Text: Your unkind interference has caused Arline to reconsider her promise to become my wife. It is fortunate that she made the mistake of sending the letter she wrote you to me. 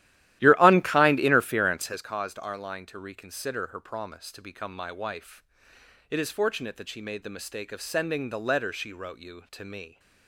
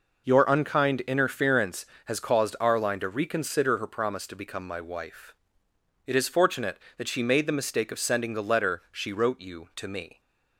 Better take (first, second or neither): second